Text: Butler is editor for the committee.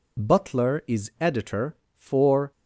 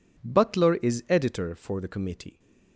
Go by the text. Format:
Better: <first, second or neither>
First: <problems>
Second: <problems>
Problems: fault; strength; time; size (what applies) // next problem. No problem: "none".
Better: second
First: stops before "the committee"; at 2.5 s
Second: none